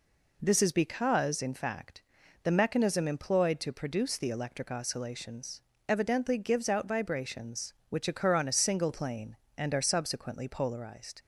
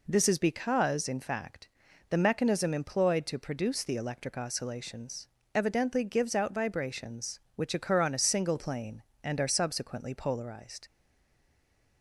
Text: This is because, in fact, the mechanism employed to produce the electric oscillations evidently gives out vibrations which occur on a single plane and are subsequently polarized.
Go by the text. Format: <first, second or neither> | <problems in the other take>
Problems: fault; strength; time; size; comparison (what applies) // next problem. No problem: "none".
first | pauses between "oscillations" and "evidently"; slight; at 5.2 s; 0.26 s long; slight in the first // stays silent after the last word; from 10.8 s on; 1.2 s long